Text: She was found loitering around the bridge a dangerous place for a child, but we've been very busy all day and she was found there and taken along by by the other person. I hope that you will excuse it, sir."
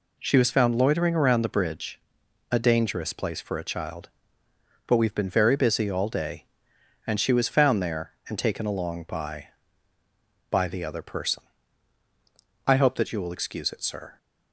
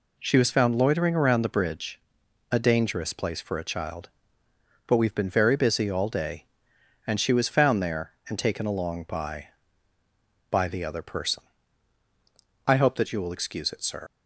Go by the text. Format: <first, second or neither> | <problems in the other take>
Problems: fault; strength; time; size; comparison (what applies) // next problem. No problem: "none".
first | pauses between "bridge" and "a"; noticeable; at 1.9 s; 0.50 s long; noticeable in the first // leaves "sir" unfinished; at 14.0 s; 110 ms